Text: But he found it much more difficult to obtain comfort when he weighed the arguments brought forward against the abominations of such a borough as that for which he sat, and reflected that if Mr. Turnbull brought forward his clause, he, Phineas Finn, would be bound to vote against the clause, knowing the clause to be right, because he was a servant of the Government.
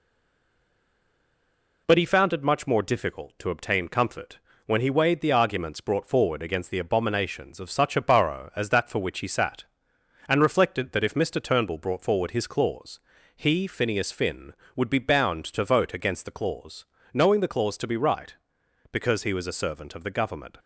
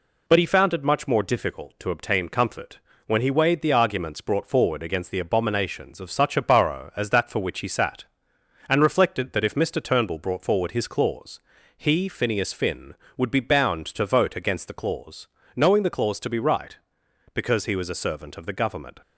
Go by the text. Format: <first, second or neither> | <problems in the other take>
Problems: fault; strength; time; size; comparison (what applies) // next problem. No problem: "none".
second | stays silent before the first word; noticeable; until 1.8 s; 1.8 s long // pauses between "comfort" and "when"; slight; at 4.3 s; 0.28 s long; slight in the second